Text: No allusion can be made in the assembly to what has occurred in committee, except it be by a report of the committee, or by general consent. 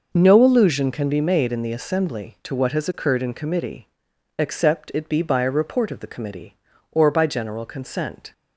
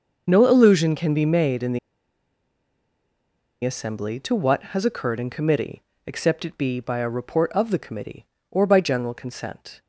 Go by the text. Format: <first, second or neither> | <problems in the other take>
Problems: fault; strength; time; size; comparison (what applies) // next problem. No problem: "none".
first | pauses between "the" and "assembly"; strong; at 1.7 s; 1.8 s long